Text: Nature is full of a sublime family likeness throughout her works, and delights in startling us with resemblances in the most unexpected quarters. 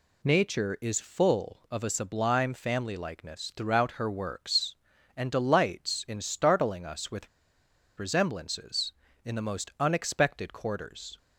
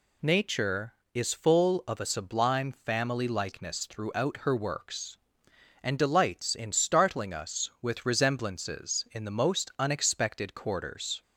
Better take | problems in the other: second | pauses between "with" and "resemblances"; noticeable; at 7.2 s; 0.69 s long

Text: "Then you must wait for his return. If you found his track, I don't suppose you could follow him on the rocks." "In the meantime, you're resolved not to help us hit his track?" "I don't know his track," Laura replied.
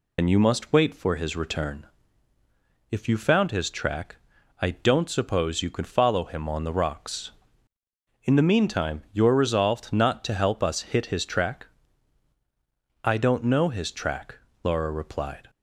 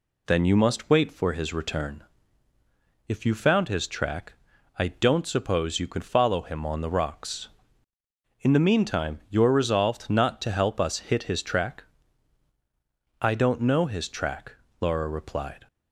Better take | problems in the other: second | loses the start of "Then"; at 0.1 s; 85 ms

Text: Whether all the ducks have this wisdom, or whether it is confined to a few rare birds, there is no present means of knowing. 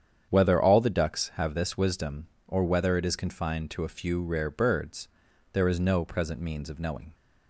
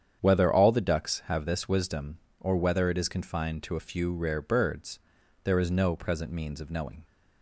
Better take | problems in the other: neither | starts louder than the rest; strong; the same in both

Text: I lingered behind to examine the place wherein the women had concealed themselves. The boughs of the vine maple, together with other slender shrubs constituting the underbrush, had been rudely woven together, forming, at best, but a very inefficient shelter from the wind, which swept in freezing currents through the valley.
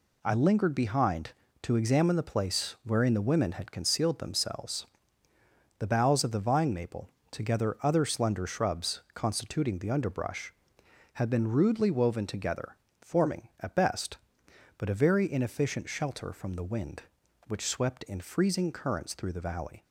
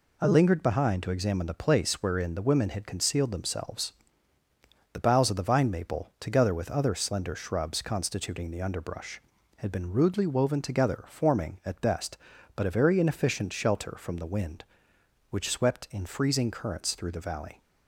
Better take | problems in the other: second | skips "with"; at 7.8 s

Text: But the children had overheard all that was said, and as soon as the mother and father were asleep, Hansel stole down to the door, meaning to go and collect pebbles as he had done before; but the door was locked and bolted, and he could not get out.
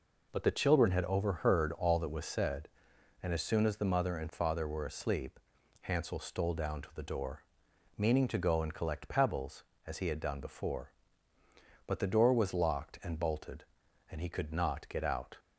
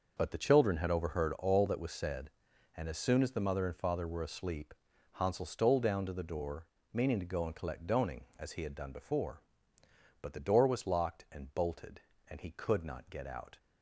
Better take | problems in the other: first | says "doning" for "pebbles"; at 7.8 s

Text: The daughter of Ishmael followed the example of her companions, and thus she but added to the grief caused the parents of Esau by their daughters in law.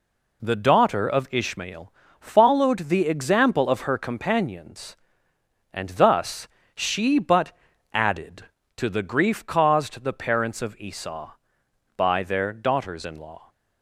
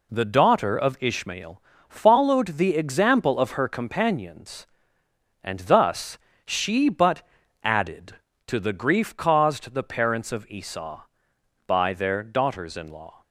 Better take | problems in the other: neither | pauses between "Ishmael" and "followed"; slight; the same in both // pauses between "thus" and "she"; slight; the same in both // pauses between "but" and "added"; the same in both

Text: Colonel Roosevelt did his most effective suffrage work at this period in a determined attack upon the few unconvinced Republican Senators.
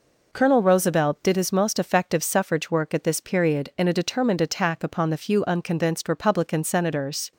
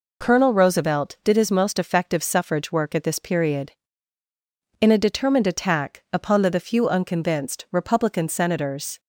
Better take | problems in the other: first | says "the" twice; at 6.4 s

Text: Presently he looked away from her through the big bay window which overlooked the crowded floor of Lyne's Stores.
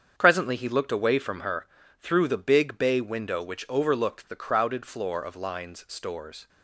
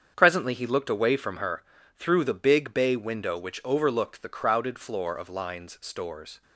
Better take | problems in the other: neither | starts louder than the rest; strong; the same in both // pauses between "her" and "through"; slight; the same in both

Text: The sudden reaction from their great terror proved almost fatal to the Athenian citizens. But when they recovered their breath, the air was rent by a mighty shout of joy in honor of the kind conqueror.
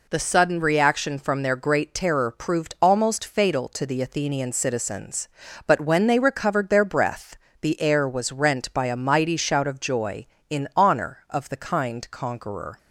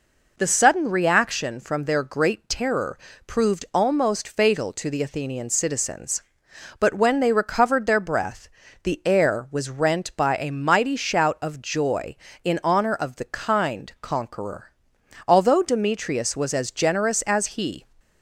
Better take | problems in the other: first | pauses between "terror" and "proved"; slight; at 2.9 s; 0.28 s long // goes on to say "Although Demetrius was as generous as he"; strong; from 15.2 s on; 2.5 s long

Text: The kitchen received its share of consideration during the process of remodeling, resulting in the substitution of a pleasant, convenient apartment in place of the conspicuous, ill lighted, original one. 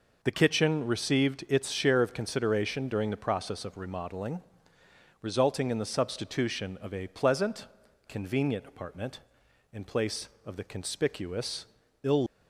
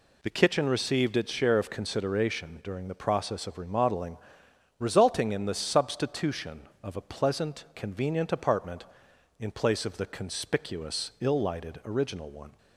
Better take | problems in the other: second | stops before "lighted original one"; at 12.2 s

